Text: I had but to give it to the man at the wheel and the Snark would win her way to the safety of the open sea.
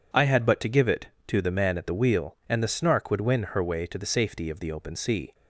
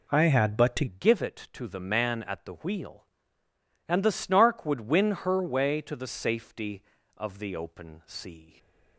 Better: first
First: none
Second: changes voice at "give"; from 0.8 s on; 7.7 s long

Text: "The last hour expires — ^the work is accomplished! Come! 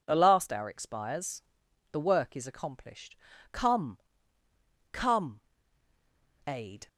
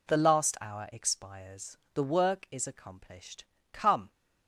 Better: second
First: goes on to say "come Aid"; strong; from 4.9 s on; 1.9 s long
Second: none

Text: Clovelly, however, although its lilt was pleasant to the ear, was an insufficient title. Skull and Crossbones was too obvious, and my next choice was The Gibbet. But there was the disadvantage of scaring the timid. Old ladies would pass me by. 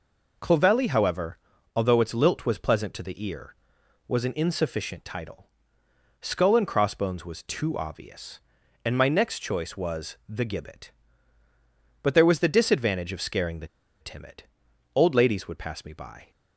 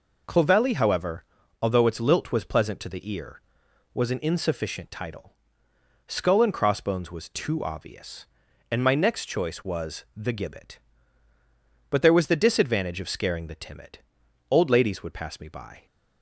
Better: second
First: pauses between "the" and "timid"; slight; at 13.6 s; 0.34 s long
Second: none

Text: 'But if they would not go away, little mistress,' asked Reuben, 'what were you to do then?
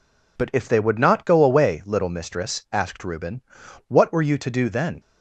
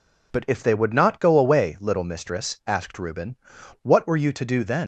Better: first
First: none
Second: leaves "then" unfinished; at 4.8 s; 80 ms

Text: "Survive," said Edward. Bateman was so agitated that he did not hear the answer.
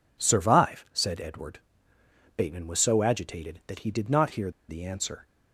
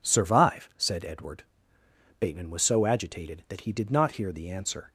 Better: second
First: pauses between "hear" and "the"; slight; at 4.4 s; 0.18 s long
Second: none

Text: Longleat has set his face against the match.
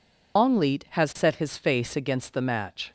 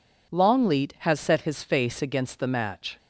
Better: second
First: loses the start of "Longleat"; at 0.3 s; 140 ms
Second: none

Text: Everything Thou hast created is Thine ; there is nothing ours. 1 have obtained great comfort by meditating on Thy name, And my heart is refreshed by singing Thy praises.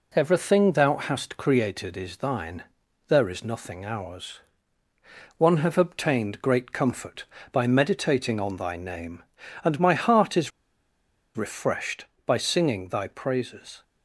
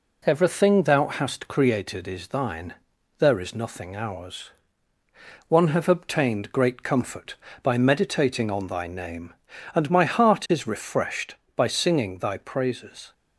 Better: second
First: pauses between "is" and "refreshed"; noticeable; at 10.5 s; 0.86 s long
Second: none

